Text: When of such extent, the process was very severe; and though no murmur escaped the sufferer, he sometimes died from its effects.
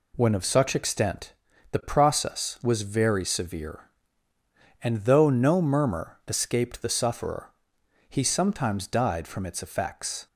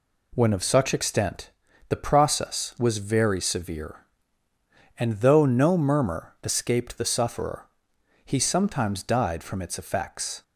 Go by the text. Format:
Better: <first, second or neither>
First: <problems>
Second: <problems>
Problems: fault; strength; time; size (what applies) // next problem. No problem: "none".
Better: neither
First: none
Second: none